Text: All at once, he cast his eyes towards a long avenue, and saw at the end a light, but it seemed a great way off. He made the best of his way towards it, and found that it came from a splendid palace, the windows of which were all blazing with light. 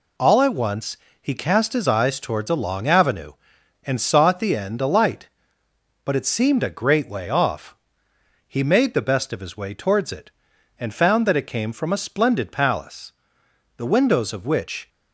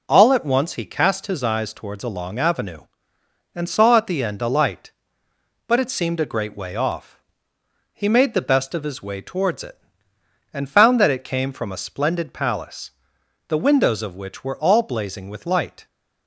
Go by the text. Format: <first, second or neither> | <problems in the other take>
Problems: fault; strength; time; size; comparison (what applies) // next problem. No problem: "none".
second | stops before "were all blazing with light"; at 14.8 s